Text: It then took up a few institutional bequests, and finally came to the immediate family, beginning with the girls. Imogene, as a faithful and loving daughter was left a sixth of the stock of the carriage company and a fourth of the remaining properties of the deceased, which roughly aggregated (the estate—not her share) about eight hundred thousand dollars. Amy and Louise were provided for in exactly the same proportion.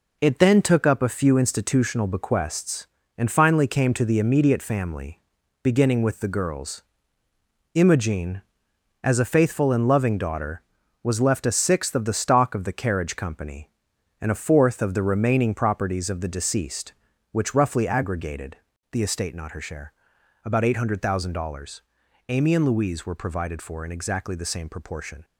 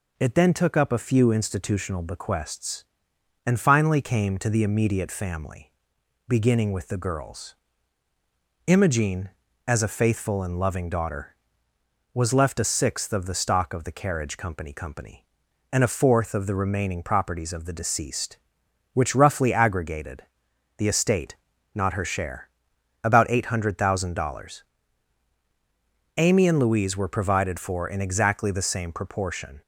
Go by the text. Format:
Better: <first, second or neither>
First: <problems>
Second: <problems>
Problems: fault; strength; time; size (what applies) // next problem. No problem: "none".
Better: first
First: none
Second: says "company" twice; at 14.7 s